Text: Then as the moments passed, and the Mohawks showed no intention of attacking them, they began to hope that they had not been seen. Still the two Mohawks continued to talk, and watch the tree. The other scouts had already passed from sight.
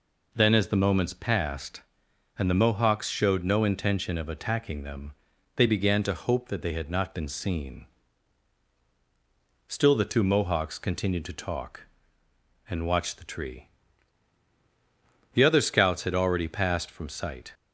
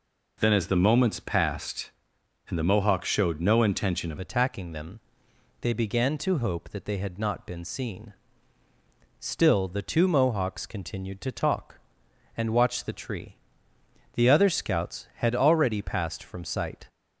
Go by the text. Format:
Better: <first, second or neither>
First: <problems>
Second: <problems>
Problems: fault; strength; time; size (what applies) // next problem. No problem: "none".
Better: first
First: none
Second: changes voice at "attacking"; from 4.1 s on; 12.7 s long